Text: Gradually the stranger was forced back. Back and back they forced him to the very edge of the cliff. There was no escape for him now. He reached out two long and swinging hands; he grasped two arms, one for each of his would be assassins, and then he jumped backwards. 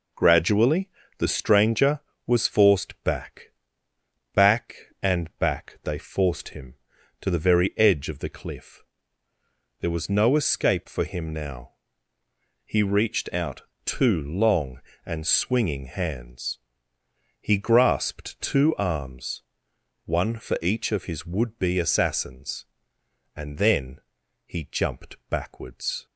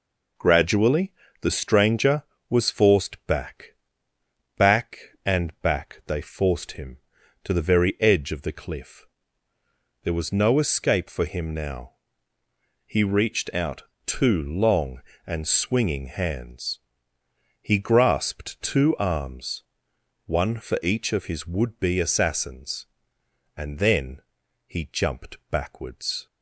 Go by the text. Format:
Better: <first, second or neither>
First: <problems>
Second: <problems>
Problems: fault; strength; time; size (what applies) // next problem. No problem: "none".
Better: neither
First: pauses between "Gradually" and "the"; slight; at 0.8 s; 0.28 s long // pauses between "out" and "two"; slight; at 13.6 s; 0.20 s long // pauses between "then" and "he"; noticeable; at 23.9 s; 0.46 s long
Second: pauses between "Gradually" and "the"; slight; at 1.1 s; 0.28 s long // pauses between "out" and "two"; slight; at 13.8 s; 0.20 s long // pauses between "then" and "he"; noticeable; at 24.2 s; 0.46 s long